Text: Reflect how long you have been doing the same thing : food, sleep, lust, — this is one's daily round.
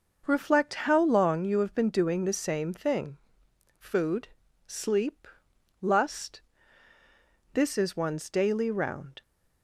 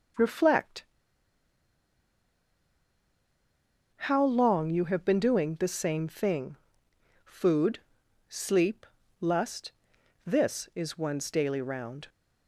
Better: first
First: none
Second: pauses between "Reflect" and "how"; strong; at 0.8 s; 3.1 s long

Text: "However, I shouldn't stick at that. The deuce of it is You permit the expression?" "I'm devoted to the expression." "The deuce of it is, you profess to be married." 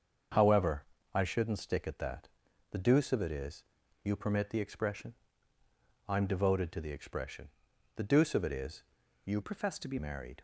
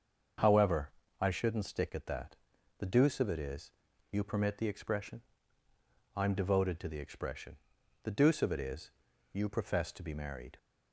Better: second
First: starts louder than the rest; until 1.6 s; 7 dB // pauses between "is" and "You"; at 3.6 s; 0.38 s long // changes voice from "profess" to "be"; from 9.4 to 9.9 s; 0.5 s long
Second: starts louder than the rest; until 1.6 s; 6.5 dB // pauses between "is" and "You"; at 3.7 s; 0.38 s long

